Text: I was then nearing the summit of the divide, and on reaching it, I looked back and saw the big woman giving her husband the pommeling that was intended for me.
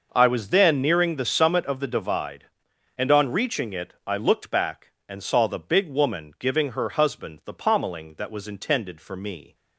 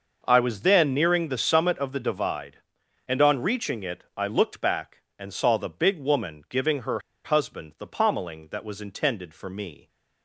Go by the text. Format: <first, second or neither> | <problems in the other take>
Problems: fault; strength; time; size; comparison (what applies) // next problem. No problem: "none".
first | pauses between "her" and "husband"; slight; at 6.9 s; 0.26 s long